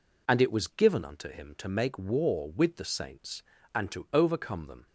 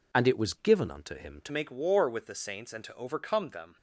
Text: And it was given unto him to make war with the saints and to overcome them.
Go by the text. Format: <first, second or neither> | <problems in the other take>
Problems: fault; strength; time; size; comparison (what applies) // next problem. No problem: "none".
first | changes voice at "make"; from 1.5 s on; 2.2 s long